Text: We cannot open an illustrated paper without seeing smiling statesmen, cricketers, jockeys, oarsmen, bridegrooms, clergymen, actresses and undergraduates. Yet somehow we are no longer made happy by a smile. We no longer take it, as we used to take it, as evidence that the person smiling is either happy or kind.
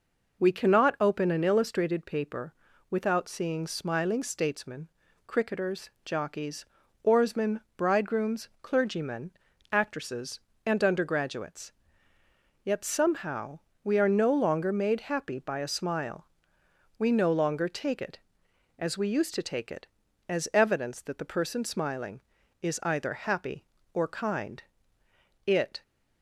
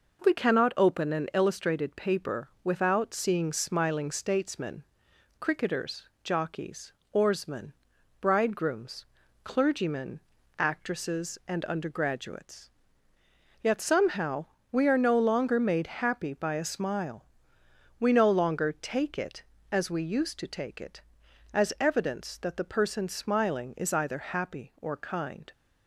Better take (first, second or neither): second